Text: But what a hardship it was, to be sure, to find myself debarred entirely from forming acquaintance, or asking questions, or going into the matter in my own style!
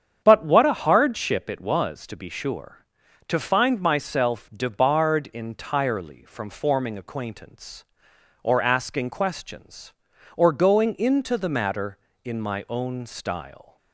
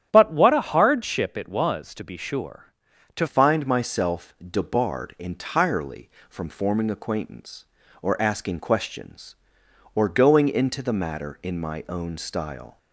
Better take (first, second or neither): first